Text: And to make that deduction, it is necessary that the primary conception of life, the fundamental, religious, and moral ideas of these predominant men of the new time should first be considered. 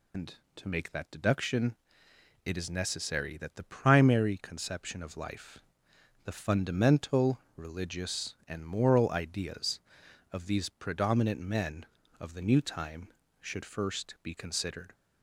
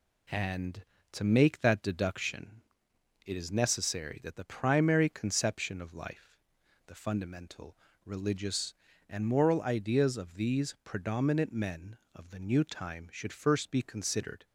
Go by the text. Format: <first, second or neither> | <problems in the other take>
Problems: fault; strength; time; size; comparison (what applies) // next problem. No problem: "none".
second | loses the start of "And"; at 0.1 s; 105 ms